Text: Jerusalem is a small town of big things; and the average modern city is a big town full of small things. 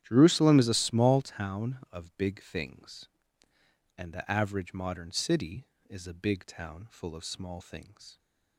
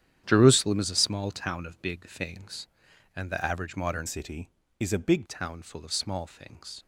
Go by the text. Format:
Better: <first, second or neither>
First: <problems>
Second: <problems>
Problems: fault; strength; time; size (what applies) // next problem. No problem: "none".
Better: first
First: starts louder than the rest; strong; until 1.0 s; 11 dB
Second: starts louder than the rest; strong; until 1.2 s; 10 dB // changes voice from "city" to "big"; from 4.0 to 5.2 s; 1.2 s long